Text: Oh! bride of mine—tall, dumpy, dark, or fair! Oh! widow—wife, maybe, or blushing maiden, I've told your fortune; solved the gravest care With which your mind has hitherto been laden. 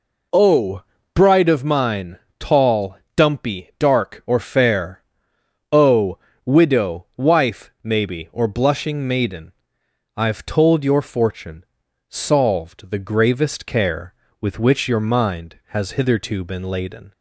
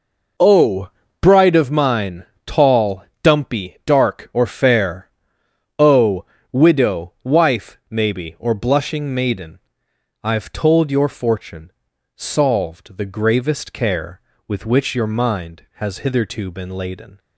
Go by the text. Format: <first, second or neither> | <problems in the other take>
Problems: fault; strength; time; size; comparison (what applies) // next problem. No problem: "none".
first | gets quieter; strong; throughout; 11 dB